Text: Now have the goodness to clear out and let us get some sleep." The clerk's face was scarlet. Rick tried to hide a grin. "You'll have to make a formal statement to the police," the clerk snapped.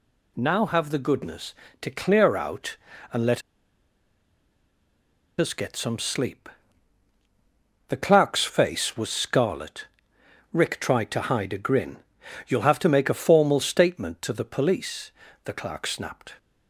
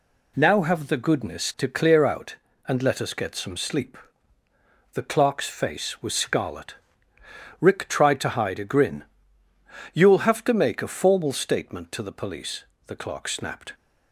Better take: second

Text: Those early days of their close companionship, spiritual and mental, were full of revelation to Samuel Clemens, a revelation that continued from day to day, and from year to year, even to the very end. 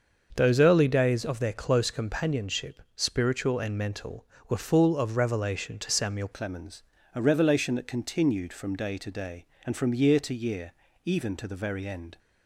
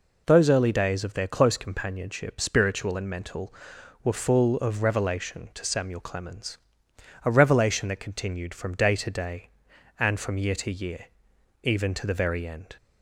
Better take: second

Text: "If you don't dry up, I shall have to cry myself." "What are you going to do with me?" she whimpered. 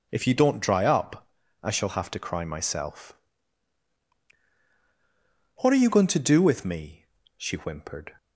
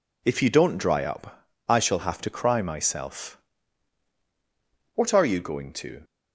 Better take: first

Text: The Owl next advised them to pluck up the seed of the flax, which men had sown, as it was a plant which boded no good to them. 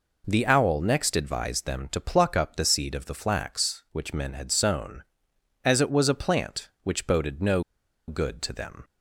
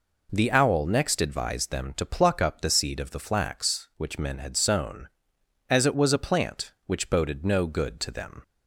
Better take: second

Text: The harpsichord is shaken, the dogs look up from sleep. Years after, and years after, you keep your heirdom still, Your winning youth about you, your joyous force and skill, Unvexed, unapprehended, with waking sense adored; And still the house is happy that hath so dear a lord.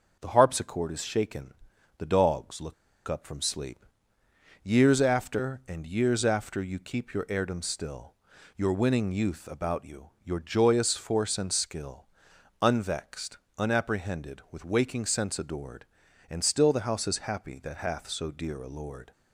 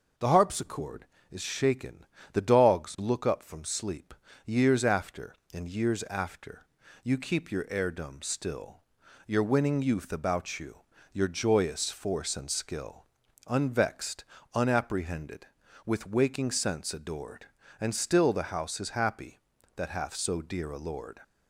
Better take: second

